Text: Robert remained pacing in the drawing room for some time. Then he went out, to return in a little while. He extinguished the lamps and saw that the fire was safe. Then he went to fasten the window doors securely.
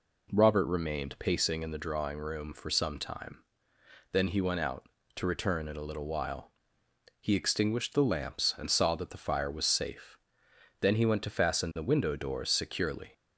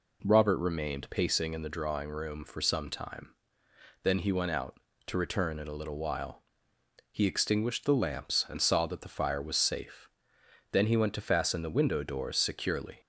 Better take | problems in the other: neither | none

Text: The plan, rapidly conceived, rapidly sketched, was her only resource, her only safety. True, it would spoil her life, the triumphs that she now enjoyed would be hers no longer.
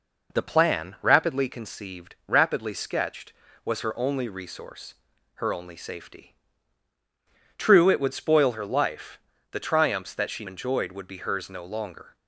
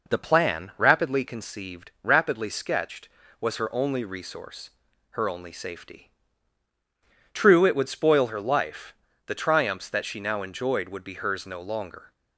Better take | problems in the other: second | skips "now"; at 10.4 s

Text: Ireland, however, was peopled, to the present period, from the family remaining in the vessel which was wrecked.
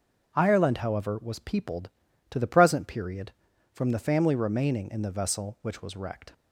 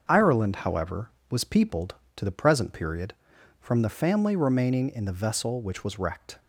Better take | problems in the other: neither | starts louder than the rest; the same in both

